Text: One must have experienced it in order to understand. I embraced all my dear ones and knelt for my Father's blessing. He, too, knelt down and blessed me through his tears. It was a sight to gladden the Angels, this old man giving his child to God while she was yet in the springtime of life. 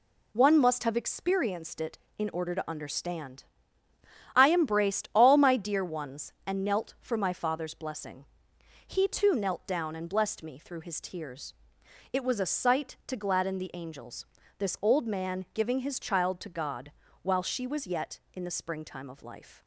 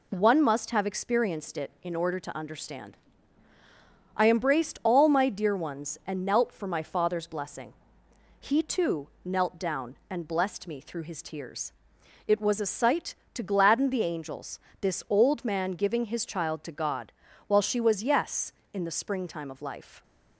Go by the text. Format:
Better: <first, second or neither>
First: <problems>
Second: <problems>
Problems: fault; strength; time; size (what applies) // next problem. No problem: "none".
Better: first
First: pauses between "God" and "while"; slight; at 16.9 s; 0.30 s long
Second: pauses between "God" and "while"; slight; at 17.1 s; 0.34 s long // says "yes" for "yet"; at 18.0 s